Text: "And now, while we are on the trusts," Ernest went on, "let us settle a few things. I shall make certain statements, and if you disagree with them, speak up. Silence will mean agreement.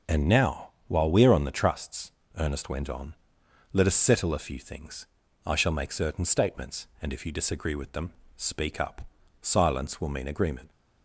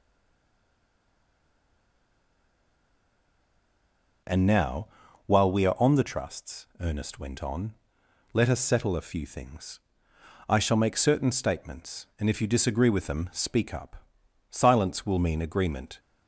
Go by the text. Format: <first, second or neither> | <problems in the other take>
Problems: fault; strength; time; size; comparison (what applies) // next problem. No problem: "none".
first | stays silent before the first word; strong; until 4.2 s; 4.2 s long